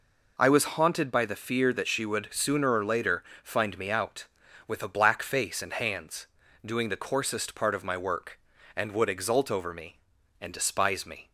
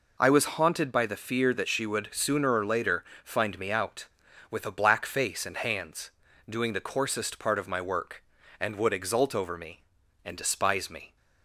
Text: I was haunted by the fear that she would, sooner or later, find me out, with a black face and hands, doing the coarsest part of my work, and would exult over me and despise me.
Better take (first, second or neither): neither